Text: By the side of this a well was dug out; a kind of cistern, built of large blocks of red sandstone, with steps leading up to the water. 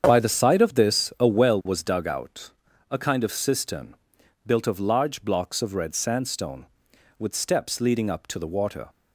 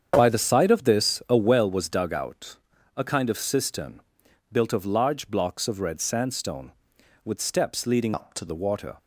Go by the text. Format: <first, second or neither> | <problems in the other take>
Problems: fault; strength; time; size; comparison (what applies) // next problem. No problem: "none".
first | starts louder than the rest; strong; until 1.1 s; 8 dB; strong in the first // changes voice from "up" to "to"; from 8.1 to 8.4 s; 0.3 s long